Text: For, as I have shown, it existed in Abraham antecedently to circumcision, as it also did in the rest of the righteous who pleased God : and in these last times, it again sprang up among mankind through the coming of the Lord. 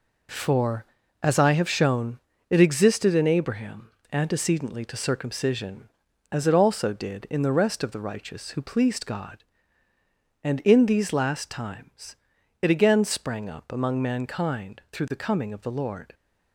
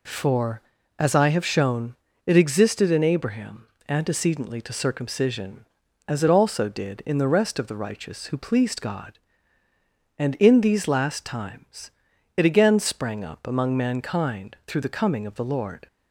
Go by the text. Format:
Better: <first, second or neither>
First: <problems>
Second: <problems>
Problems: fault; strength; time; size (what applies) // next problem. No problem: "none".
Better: second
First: gets quieter; strong; throughout; 7.5 dB // pauses between "Abraham" and "antecedently"; slight; at 3.8 s; 0.22 s long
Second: pauses between "Abraham" and "antecedently"; slight; at 3.6 s; 0.22 s long